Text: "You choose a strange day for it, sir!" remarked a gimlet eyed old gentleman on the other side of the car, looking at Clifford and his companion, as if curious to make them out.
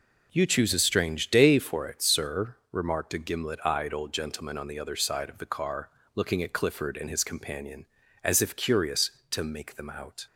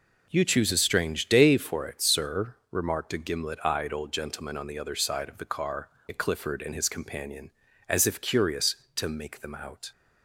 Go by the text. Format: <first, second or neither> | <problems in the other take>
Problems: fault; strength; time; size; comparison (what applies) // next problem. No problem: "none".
first | skips "looking"; at 5.9 s